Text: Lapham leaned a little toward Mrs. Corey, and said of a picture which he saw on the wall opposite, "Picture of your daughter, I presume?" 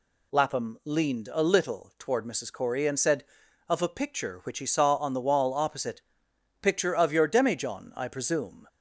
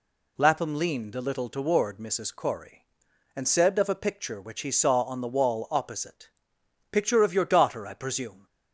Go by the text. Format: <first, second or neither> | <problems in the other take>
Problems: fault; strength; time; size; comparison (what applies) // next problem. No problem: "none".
second | says "demijohn" for "daughter"; at 7.2 s